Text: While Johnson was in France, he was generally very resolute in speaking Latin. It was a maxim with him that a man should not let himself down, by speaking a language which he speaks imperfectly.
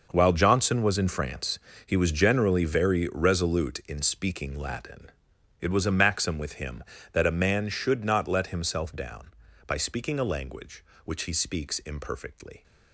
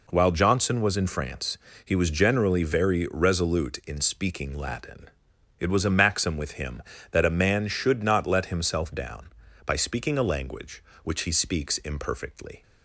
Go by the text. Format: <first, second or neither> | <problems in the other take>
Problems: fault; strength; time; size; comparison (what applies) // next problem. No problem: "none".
second | gets quieter; strong; throughout; 14 dB